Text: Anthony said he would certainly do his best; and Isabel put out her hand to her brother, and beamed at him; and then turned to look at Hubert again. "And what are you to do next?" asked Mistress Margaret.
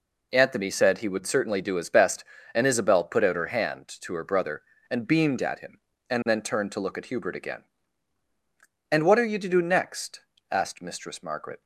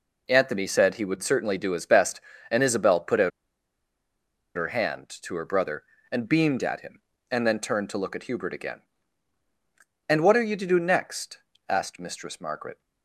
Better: first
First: none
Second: pauses between "out" and "her"; strong; at 3.3 s; 1.2 s long

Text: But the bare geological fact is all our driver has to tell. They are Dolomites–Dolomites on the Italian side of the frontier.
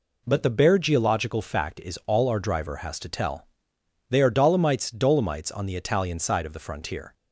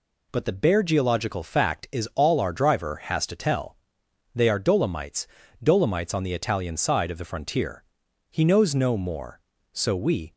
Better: first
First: none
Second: goes on to say "He knows no more so we"; strong; from 8.2 s on; 2.0 s long

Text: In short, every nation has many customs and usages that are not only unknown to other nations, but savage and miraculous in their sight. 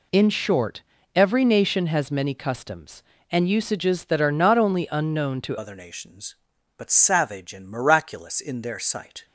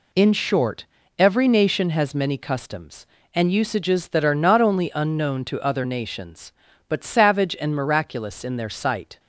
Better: second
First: changes voice at "other"; from 5.5 s on; 3.7 s long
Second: none

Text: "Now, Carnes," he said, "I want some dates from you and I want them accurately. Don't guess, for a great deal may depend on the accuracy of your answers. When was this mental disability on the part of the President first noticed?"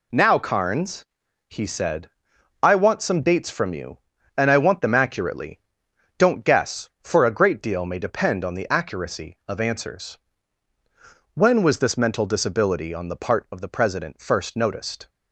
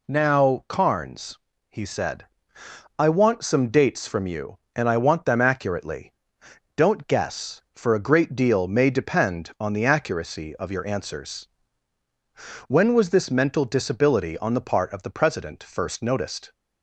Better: second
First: skips "your"; at 9.5 s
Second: none

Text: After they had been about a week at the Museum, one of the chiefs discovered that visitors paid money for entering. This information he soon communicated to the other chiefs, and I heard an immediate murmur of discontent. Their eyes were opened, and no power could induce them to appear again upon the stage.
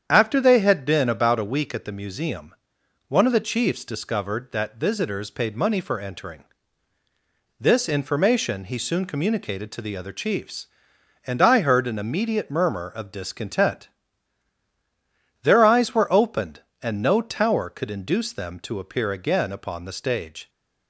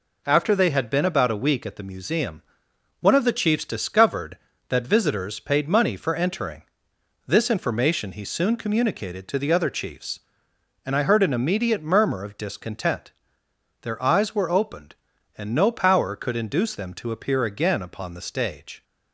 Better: second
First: starts louder than the rest; strong; until 1.0 s; 8.5 dB // says "tower" for "power"; at 17.2 s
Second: none

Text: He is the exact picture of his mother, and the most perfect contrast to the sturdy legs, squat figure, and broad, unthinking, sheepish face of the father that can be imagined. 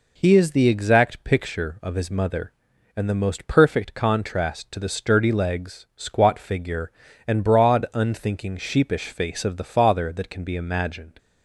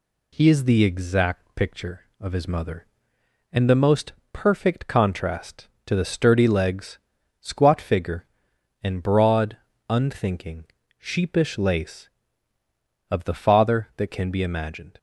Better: first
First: none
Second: pauses between "most" and "perfect"; slight; at 4.1 s; 0.18 s long // says "lace" for "face"; at 11.5 s

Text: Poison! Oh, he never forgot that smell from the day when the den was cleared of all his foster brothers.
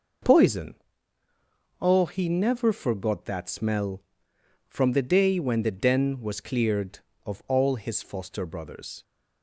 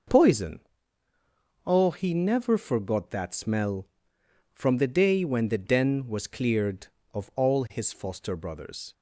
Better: neither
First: none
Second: none

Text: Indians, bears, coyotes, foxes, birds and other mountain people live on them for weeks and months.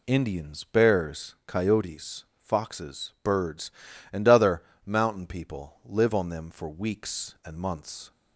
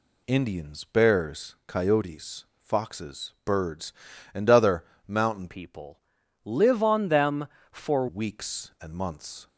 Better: first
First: pauses between "other" and "mountain"; slight; at 4.6 s; 0.22 s long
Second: pauses between "other" and "mountain"; slight; at 4.8 s; 0.22 s long // changes voice from "people" to "for"; from 5.4 to 8.0 s; 2.6 s long // pauses between "people" and "live"; at 6.0 s; 0.44 s long

